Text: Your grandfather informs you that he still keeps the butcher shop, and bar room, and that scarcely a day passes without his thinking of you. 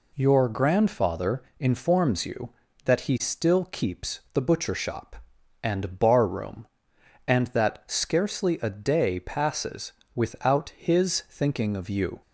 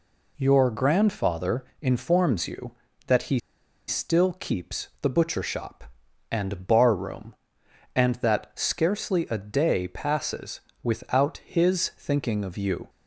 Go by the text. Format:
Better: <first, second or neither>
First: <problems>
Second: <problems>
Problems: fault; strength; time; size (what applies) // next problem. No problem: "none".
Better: first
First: pauses between "grandfather" and "informs"; slight; at 1.4 s; 0.16 s long // pauses between "passes" and "without"; slight; at 9.9 s; 0.22 s long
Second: pauses between "grandfather" and "informs"; slight; at 1.6 s; 0.16 s long // pauses between "he" and "still"; noticeable; at 3.3 s; 0.49 s long // pauses between "passes" and "without"; slight; at 10.5 s; 0.22 s long